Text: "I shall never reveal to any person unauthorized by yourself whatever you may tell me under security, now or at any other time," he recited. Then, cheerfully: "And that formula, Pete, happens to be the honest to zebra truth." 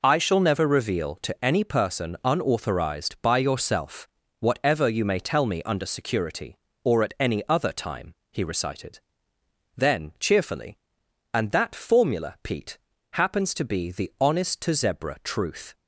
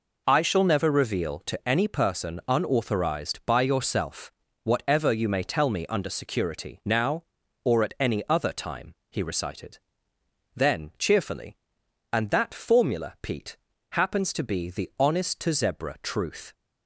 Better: second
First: pauses between "yourself" and "whatever"; slight; at 4.0 s; 0.32 s long // skips "now"; at 6.7 s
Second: pauses between "yourself" and "whatever"; slight; at 4.3 s; 0.32 s long

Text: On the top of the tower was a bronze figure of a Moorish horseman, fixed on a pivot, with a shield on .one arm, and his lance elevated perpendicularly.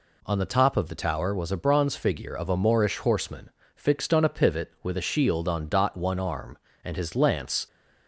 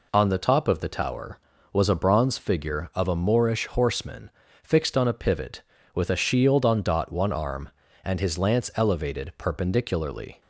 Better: second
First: stops before "elevated perpendicularly"; at 7.6 s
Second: none

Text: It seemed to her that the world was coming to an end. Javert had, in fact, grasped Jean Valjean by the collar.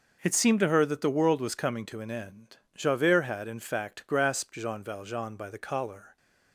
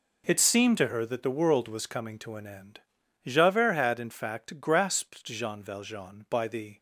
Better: first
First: none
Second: stops before "collar"; at 6.7 s

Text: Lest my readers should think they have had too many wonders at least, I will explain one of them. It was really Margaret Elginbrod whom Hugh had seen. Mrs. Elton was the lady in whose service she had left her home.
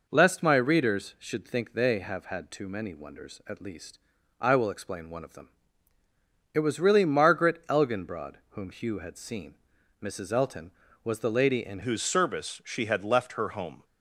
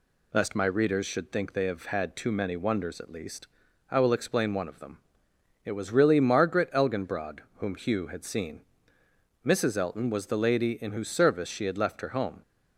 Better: second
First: pauses between "Elginbrod" and "whom"; slight; at 8.3 s; 0.16 s long // changes voice at "whose"; from 11.8 s on; 2.0 s long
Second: pauses between "Elginbrod" and "whom"; slight; at 7.3 s; 0.18 s long

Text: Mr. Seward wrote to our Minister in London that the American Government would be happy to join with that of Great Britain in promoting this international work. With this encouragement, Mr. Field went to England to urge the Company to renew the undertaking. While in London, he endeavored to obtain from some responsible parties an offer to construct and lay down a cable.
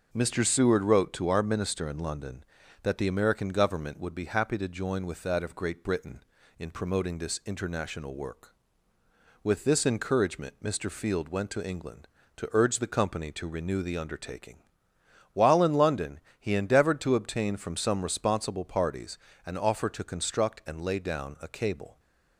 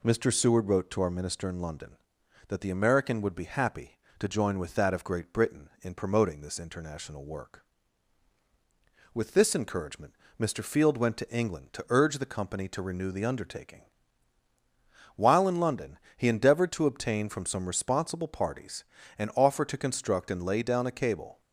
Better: first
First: pauses between "parties" and "an"; slight; at 19.1 s; 0.28 s long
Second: skips "Government"; at 3.2 s // pauses between "parties" and "an"; slight; at 18.8 s; 0.34 s long

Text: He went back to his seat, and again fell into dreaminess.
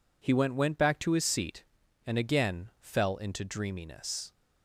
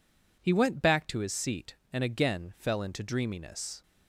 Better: second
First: says "went" twice; at 0.5 s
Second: none

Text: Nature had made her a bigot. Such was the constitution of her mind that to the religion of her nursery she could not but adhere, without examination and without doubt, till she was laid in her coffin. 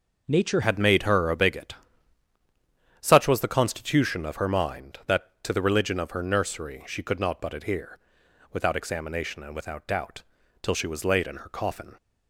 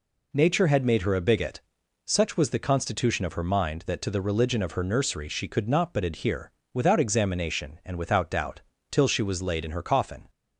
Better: second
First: changes voice at "had"; from 0.6 s on; 11.3 s long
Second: none

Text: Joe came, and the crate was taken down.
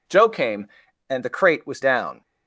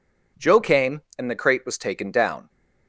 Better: second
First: skips "taken"; at 1.8 s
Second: none

